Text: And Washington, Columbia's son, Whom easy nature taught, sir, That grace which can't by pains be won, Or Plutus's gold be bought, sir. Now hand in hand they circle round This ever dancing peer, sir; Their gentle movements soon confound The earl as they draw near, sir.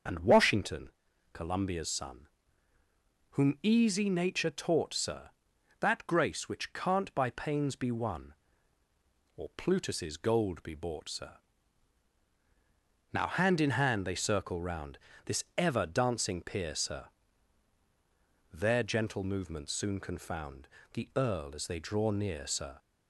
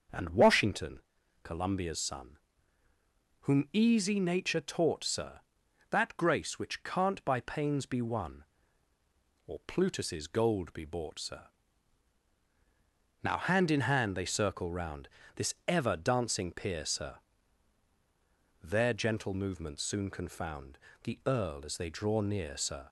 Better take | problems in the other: second | loses the start of "And"; at 0.0 s; 65 ms // starts louder than the rest; until 1.4 s; 6.5 dB; also in the second // pauses between "round" and "This"; slight; at 14.9 s; 0.30 s long; slight in the second // pauses between "confound" and "The"; slight; at 20.6 s; 0.28 s long; slight in the second

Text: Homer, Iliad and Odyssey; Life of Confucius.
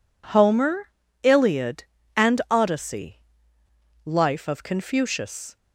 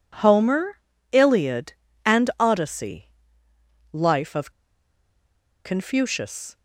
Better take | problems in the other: first | pauses between "of" and "Confucius"; at 4.4 s; 1.1 s long

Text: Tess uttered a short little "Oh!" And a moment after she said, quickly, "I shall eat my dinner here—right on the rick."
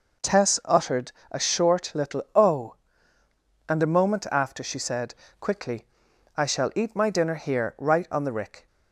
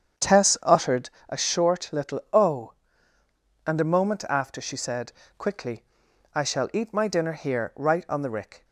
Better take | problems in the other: first | starts louder than the rest; strong; until 1.3 s; 8 dB // pauses between "uttered" and "a"; slight; at 1.1 s; 0.18 s long; slight in the first

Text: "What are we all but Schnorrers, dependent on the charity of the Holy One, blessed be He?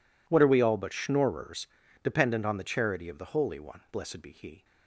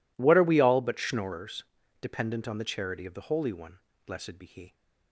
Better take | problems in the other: neither | none

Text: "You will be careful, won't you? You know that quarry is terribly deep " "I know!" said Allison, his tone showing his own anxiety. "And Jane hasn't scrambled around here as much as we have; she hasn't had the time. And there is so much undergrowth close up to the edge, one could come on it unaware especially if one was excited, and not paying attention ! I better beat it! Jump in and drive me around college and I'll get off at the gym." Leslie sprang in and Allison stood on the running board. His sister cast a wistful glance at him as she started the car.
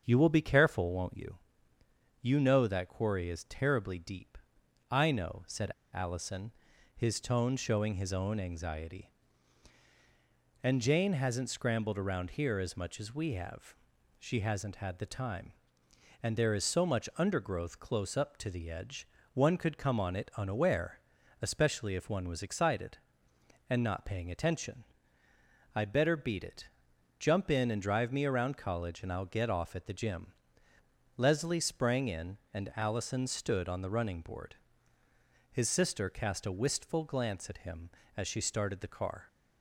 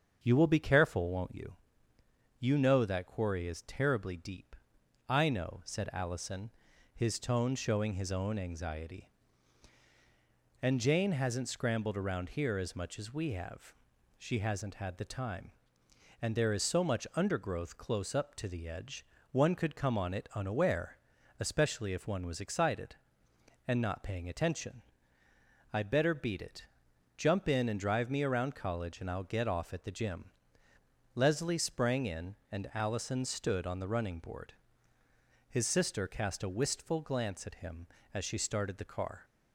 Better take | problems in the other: second | starts louder than the rest; strong; until 1.0 s; 7.5 dB; strong in the second // pauses between "said" and "Allison"; slight; at 5.7 s; 0.23 s long // pauses between "unaware" and "especially"; at 20.9 s; 0.42 s long; also in the second

